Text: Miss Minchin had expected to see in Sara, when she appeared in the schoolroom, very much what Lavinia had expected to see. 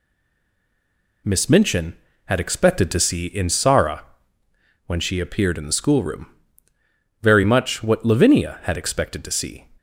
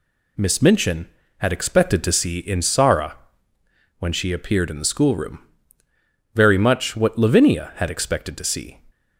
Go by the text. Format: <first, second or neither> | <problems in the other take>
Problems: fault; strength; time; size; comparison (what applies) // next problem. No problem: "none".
second | stays silent before the first word; noticeable; until 1.2 s; 1.2 s long